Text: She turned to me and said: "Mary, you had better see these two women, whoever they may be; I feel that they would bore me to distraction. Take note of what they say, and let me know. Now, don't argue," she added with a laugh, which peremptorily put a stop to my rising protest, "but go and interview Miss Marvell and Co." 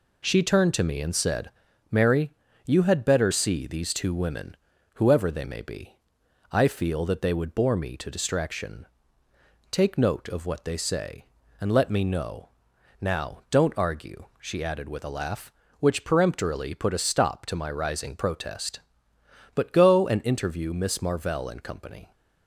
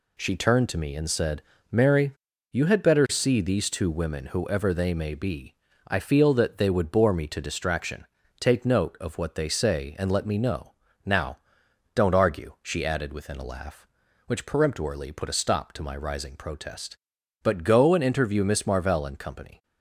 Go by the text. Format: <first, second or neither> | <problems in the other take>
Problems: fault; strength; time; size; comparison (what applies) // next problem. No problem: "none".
first | says "within" for "with"; at 13.1 s